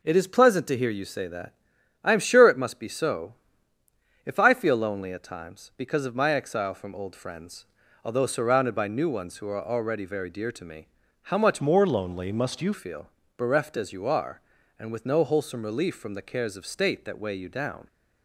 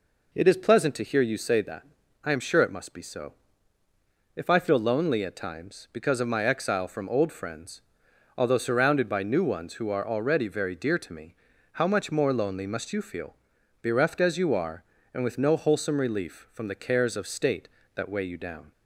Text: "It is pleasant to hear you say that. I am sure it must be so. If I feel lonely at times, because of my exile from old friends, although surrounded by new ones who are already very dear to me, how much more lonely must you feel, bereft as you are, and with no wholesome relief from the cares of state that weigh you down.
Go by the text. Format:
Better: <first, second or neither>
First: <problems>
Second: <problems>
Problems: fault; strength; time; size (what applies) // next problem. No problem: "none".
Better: second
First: changes voice from "more" to "you"; from 11.6 to 12.7 s; 1.1 s long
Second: none